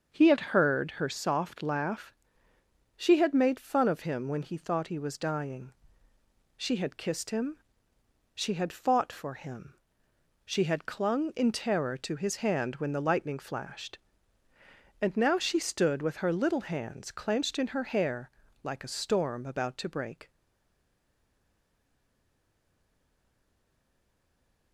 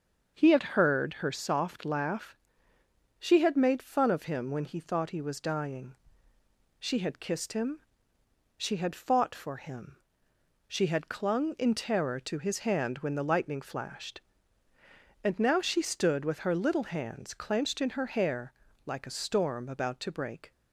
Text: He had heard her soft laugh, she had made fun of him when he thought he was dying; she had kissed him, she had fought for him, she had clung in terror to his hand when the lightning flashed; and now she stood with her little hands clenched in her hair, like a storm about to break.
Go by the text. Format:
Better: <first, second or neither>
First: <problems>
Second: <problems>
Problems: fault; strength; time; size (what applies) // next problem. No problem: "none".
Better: second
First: starts louder than the rest; until 1.2 s; 6.5 dB // stays silent after the last word; strong; from 20.2 s on; 4.5 s long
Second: starts louder than the rest; until 1.4 s; 6.5 dB